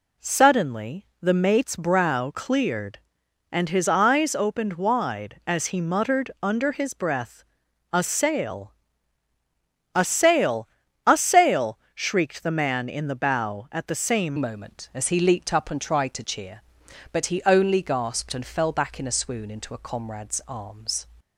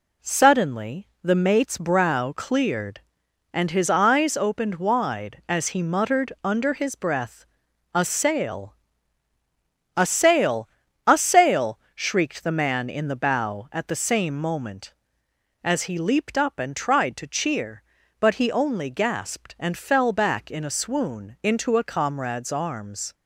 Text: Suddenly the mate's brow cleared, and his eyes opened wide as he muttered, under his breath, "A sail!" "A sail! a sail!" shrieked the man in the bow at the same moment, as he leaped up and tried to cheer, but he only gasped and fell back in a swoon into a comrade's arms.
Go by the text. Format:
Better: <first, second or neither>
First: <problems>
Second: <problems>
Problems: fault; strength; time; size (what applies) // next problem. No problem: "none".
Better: second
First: changes voice at "moment"; from 14.3 s on; 6.7 s long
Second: none